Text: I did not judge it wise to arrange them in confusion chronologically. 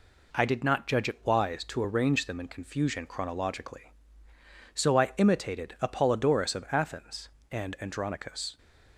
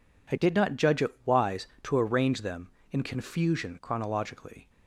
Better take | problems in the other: second | goes on to say "So I imitated Apollodorus of Athens and Andronicus"; strong; from 4.7 s on; 3.8 s long

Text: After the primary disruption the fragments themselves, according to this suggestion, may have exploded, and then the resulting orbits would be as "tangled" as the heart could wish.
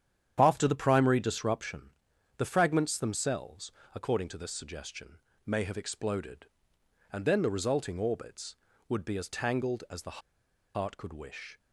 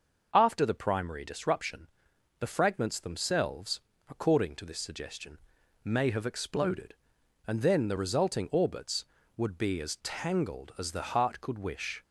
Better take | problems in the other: second | starts louder than the rest; strong; until 1.4 s; 9 dB // pauses between "disruption" and "the"; noticeable; at 1.9 s; 0.46 s long; noticeable in the second // pauses between "the" and "heart"; noticeable; at 10.2 s; 0.55 s long

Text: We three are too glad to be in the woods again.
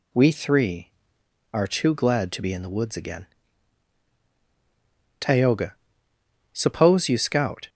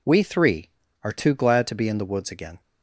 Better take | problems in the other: second | goes on to say "Tayoga suppose you scout"; strong; from 5.1 s on; 2.4 s long

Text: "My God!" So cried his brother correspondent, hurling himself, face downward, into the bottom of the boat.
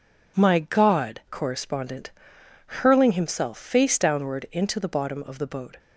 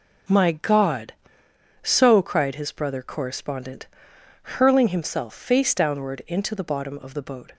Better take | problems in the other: second | skips "So cried his brother"; at 1.2 s

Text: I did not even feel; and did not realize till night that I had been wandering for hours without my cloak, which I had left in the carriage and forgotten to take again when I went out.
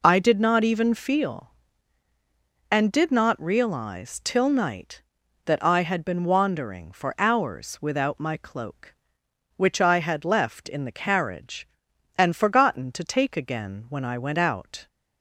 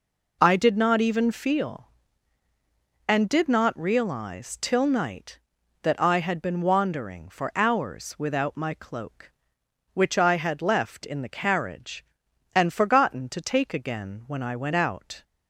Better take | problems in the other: neither | none

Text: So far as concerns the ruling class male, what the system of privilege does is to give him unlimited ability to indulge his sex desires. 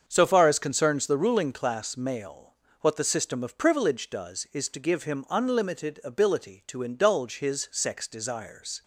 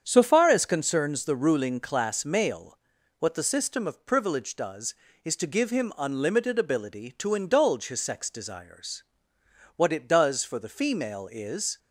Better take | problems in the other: first | starts louder than the rest; strong; until 1.0 s; 8 dB; also in the first // goes on to say "What it does for the female is"; strong; from 9.7 s on; 2.0 s long

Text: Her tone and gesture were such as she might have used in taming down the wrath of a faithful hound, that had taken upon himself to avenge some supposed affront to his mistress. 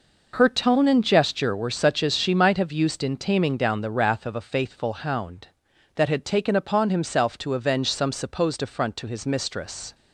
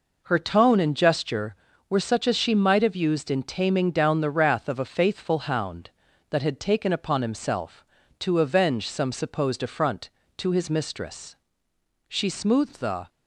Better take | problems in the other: first | goes on to say "She smoothed the"; noticeable; from 12.0 s on; 1.0 s long

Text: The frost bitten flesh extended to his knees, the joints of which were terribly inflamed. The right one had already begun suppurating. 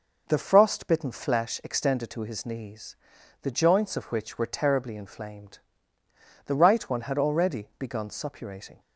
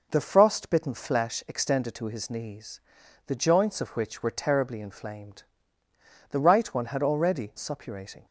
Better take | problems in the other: first | skips "begun"; at 7.5 s

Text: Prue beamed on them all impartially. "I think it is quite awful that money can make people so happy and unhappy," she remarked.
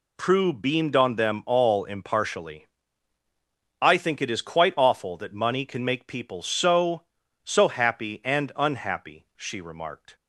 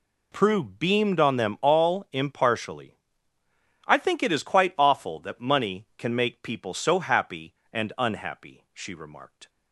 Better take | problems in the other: second | says "so" twice; at 7.4 s

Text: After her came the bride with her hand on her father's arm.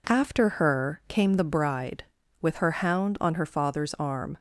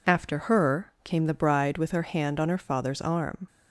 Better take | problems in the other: second | says "hound" for "hand"; at 2.8 s

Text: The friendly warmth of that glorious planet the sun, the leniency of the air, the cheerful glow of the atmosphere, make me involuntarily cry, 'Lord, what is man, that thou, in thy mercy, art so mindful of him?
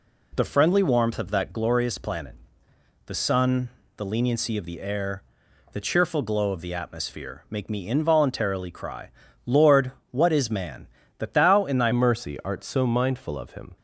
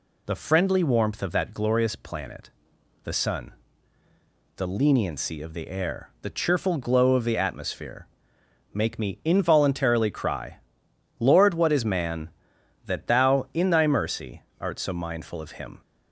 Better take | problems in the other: second | pauses between "planet" and "the"; noticeable; at 2.3 s; 0.72 s long; noticeable in the second // changes voice at "mercy"; from 11.9 s on; 1.8 s long

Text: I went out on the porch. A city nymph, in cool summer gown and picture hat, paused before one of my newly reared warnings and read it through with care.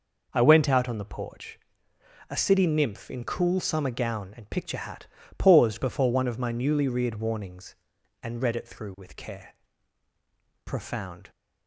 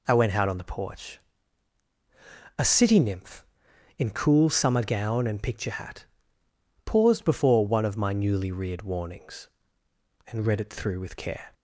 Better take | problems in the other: second | goes on to say "Profound"; noticeable; from 10.6 s on; 0.66 s long

